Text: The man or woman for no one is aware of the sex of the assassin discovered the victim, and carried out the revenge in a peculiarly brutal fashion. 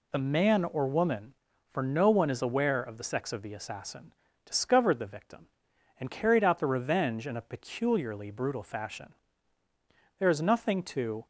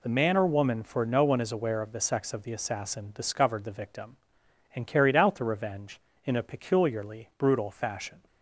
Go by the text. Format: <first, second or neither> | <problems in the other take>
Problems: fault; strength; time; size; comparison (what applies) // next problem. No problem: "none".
second | pauses between "assassin" and "discovered"; slight; at 4.1 s; 0.32 s long // goes on to say "There is nothing to"; noticeable; from 10.1 s on; 1.0 s long